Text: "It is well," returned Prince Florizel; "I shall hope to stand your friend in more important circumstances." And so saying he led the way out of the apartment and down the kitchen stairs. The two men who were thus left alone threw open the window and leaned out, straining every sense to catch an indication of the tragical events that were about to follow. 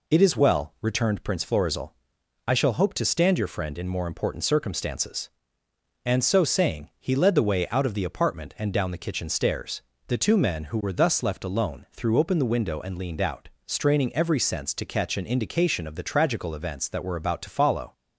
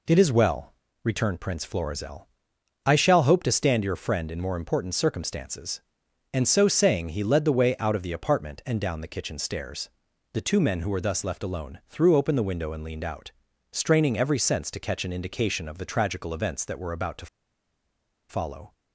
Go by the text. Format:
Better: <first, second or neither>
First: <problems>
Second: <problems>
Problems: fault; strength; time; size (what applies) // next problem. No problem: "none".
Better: first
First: none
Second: pauses between "to" and "follow"; at 17.2 s; 1.0 s long